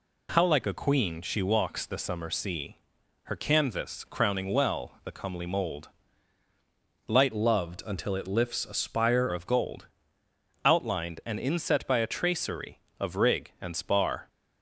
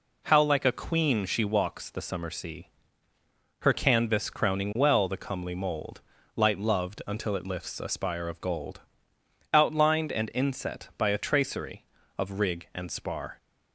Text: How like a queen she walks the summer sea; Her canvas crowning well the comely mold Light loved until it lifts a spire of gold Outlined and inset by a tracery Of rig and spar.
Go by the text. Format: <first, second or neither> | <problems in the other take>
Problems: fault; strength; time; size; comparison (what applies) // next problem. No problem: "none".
second | pauses between "mold" and "Light"; at 5.8 s; 1.2 s long; slight in the second // changes voice from "loved" to "spire"; from 7.3 to 9.2 s; 1.9 s long // pauses between "gold" and "Outlined"; noticeable; at 9.8 s; 0.76 s long; noticeable in the second